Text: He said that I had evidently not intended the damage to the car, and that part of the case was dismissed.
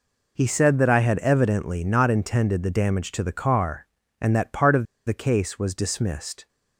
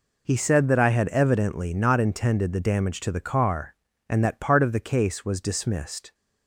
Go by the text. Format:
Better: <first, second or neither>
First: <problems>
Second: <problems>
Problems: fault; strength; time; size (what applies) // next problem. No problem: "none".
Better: second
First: pauses between "of" and "the"; slight; at 4.8 s; 0.22 s long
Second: none